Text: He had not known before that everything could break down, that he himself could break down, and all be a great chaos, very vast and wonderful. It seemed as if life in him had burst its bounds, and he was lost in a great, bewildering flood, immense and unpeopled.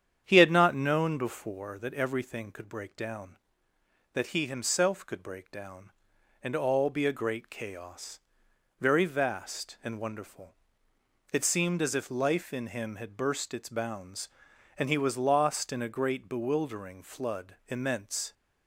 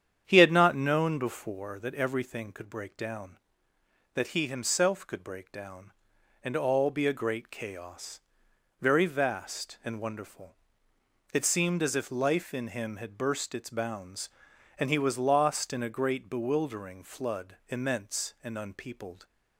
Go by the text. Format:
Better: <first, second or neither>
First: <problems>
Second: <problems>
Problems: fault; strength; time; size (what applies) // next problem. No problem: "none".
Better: second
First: starts louder than the rest; strong; until 1.2 s; 8.5 dB // stops before "and unpeopled"; at 18.3 s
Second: starts louder than the rest; strong; until 1.2 s; 8.5 dB